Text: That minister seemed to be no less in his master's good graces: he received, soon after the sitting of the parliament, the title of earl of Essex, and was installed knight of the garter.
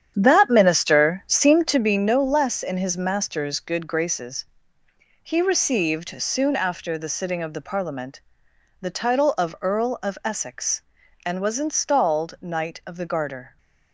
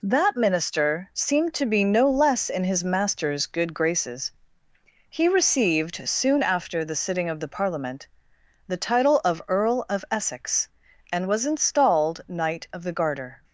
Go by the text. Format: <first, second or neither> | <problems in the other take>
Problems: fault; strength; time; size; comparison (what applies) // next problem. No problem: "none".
second | starts louder than the rest; strong; until 1.9 s; 9 dB